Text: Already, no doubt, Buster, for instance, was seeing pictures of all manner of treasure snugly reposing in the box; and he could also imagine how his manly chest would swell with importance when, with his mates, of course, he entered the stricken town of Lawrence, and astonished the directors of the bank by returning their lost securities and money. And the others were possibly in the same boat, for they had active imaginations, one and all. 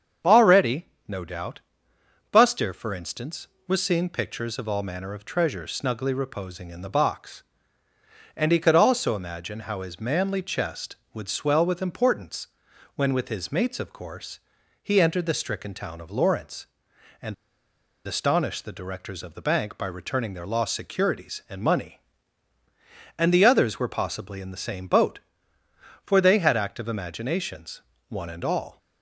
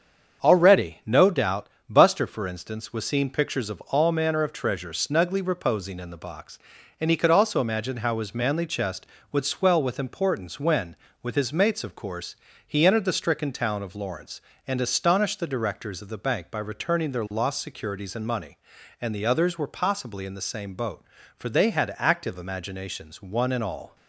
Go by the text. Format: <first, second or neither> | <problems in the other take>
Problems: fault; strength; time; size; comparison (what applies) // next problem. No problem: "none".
second | starts louder than the rest; strong; until 1.4 s; 7 dB; also in the second // pauses between "importance" and "when"; noticeable; at 12.4 s; 0.48 s long // pauses between "and" and "astonished"; noticeable; at 17.3 s; 0.73 s long